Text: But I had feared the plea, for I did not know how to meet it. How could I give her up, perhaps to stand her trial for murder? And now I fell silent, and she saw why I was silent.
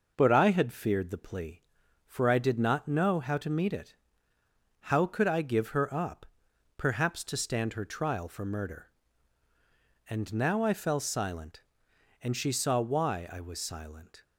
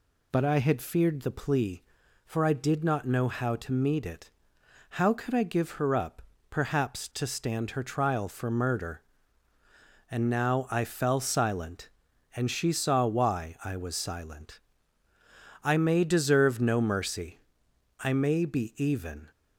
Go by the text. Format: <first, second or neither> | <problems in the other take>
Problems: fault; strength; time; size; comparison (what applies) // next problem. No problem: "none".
first | goes on to say "I may deserve no mercy I may be even"; strong; from 15.6 s on; 3.6 s long